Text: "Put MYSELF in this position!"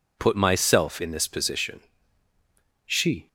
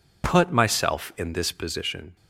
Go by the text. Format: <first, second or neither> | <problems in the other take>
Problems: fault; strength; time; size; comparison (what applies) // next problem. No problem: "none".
second | goes on to say "She"; slight; from 2.8 s on; 0.42 s long